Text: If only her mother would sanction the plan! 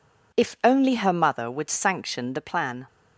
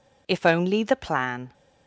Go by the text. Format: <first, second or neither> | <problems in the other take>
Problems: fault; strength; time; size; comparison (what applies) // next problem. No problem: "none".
first | skips "her mother would sanction"; at 0.8 s